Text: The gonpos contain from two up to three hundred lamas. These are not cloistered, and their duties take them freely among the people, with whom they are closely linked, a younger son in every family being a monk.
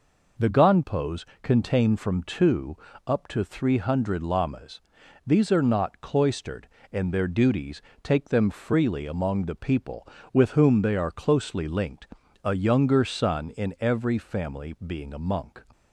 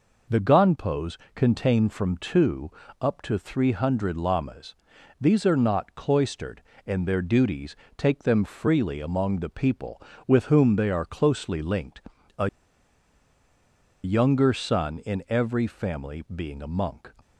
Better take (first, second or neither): first